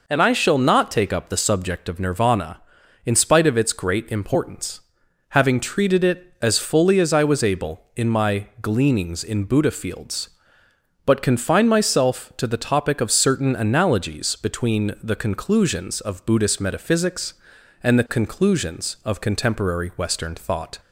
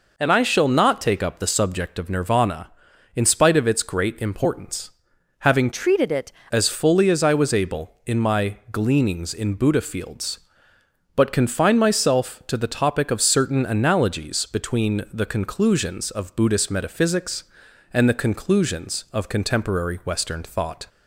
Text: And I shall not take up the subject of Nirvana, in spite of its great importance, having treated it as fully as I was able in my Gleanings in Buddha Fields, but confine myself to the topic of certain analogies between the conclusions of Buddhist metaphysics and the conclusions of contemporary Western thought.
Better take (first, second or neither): first